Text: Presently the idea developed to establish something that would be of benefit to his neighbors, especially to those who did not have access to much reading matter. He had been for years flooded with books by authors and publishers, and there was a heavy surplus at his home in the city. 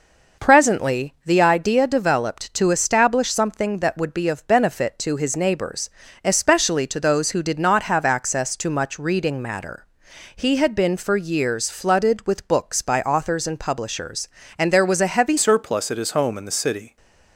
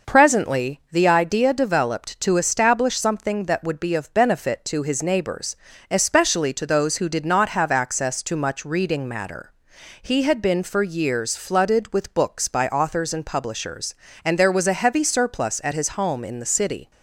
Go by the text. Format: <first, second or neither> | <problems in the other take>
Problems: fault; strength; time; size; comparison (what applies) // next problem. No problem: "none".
second | changes voice at "surplus"; from 15.3 s on; 1.6 s long